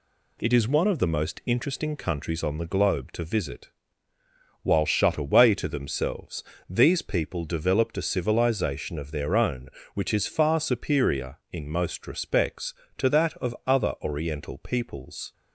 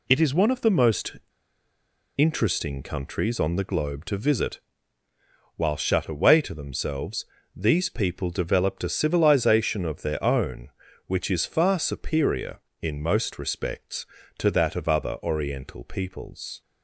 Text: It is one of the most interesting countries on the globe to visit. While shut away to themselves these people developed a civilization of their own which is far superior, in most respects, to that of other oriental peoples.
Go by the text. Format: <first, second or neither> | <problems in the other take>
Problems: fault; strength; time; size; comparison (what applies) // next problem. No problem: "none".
first | pauses between "most" and "interesting"; at 1.1 s; 1.0 s long // pauses between "themselves" and "these"; slight; at 7.2 s; 0.30 s long; slight in the first